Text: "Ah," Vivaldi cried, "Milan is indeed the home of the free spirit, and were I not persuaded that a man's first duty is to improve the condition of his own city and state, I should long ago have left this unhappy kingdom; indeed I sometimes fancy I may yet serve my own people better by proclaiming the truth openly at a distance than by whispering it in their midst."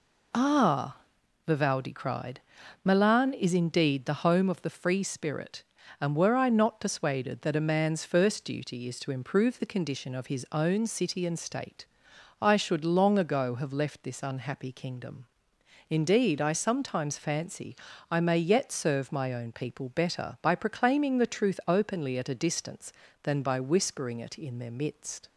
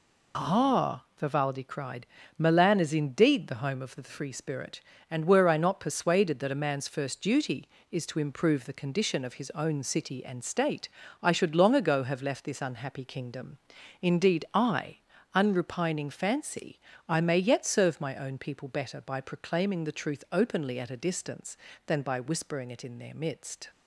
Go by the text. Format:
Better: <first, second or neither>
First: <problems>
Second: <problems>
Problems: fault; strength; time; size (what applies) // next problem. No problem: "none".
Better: first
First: pauses between "fancy" and "I"; slight; at 17.7 s; 0.34 s long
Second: says "unrepining" for "sometimes"; at 15.3 s // pauses between "fancy" and "I"; slight; at 16.7 s; 0.28 s long